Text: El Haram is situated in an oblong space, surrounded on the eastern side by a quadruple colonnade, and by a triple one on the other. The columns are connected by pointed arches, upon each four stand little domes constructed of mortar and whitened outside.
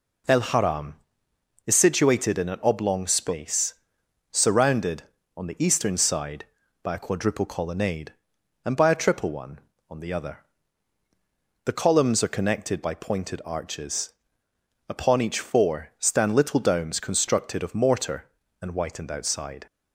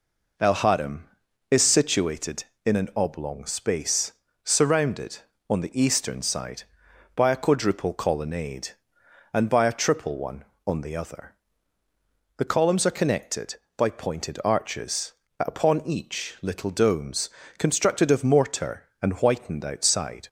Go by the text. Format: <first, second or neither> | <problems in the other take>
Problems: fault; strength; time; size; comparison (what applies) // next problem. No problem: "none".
first | skips "four stand"; at 16.3 s // pauses between "domes" and "constructed"; slight; at 17.2 s; 0.28 s long